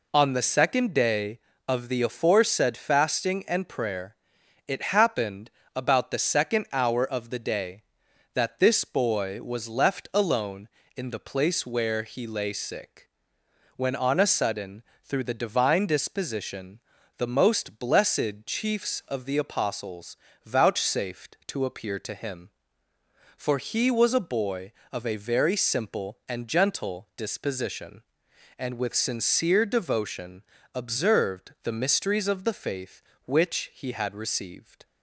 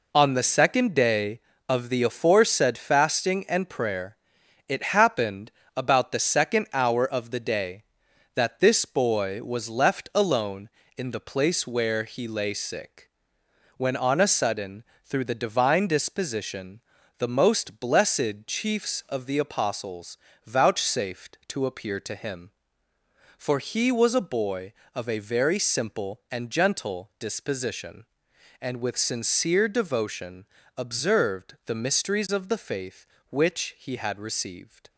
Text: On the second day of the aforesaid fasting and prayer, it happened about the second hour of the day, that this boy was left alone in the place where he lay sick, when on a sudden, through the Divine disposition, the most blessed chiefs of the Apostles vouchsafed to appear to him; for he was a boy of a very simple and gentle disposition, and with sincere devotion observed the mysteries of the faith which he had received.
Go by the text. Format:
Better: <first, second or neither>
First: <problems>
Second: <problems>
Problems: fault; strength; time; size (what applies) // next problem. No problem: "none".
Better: first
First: pauses between "happened" and "about"; slight; at 5.5 s; 0.24 s long // pauses between "Apostles" and "vouchsafed"; slight; at 20.1 s; 0.26 s long // pauses between "devotion" and "observed"; slight; at 30.4 s; 0.32 s long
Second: gets quieter; strong; throughout; 7.5 dB // pauses between "happened" and "about"; slight; at 5.5 s; 0.24 s long // pauses between "Apostles" and "vouchsafed"; slight; at 20.1 s; 0.26 s long // pauses between "devotion" and "observed"; slight; at 30.4 s; 0.32 s long